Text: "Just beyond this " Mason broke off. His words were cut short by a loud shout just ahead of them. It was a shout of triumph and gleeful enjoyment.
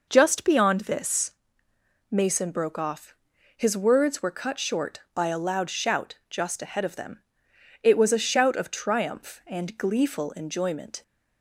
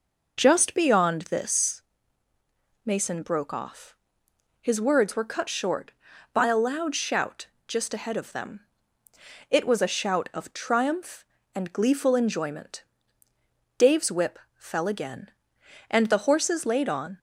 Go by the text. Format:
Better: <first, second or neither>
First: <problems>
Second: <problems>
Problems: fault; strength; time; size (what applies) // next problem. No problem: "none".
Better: first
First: none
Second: pauses between "shout" and "just"; slight; at 7.4 s; 0.18 s long // goes on to say "Dave's whip fell again and the horses laid on"; strong; from 13.7 s on; 3.4 s long